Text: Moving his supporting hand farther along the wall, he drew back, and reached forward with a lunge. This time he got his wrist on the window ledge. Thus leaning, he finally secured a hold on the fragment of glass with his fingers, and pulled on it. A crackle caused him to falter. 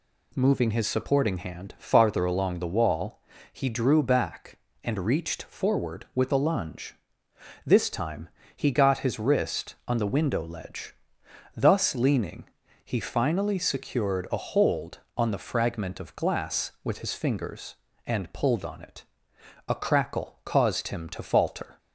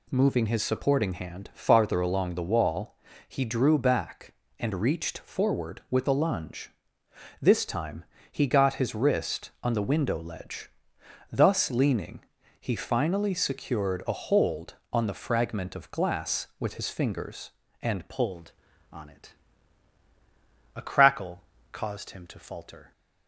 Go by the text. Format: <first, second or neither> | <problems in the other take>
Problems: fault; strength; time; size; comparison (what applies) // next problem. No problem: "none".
first | pauses between "time" and "he"; slight; at 8.0 s; 0.28 s long; slight in the first // changes voice at "pulled"; from 18.0 s on; 4.9 s long // pauses between "crackle" and "caused"; slight; at 21.4 s; 0.28 s long